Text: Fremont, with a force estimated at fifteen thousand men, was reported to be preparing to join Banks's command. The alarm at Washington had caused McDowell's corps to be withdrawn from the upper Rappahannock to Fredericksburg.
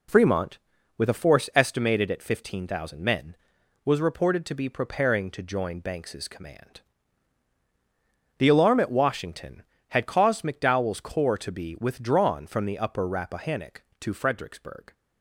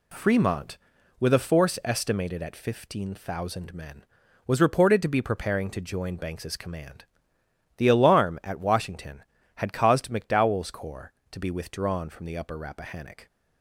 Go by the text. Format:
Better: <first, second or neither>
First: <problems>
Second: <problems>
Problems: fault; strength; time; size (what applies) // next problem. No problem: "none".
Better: first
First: none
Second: stops before "to Fredericksburg"; at 13.2 s